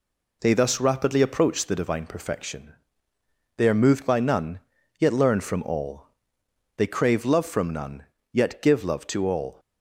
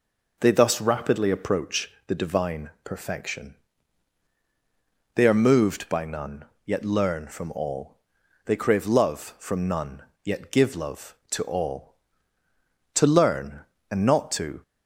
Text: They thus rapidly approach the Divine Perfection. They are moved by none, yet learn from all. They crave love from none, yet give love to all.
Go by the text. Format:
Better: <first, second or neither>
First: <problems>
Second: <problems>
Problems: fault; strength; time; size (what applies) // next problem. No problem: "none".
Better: first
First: none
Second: pauses between "approach" and "the"; slight; at 1.8 s; 0.16 s long // goes on to say "To learn and not to"; strong; from 12.9 s on; 1.6 s long